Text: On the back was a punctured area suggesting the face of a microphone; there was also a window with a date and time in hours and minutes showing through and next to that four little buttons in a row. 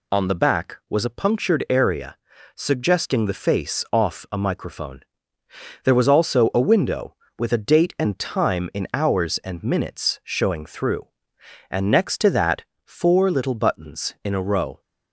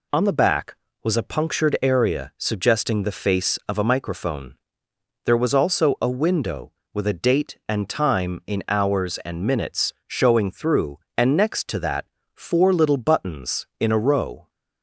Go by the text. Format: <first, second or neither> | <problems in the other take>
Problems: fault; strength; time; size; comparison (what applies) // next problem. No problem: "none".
second | pauses between "area" and "suggesting"; at 2.1 s; 0.42 s long // says "off" for "of"; at 3.9 s // pauses between "that" and "four"; slight; at 12.6 s; 0.22 s long; slight in the second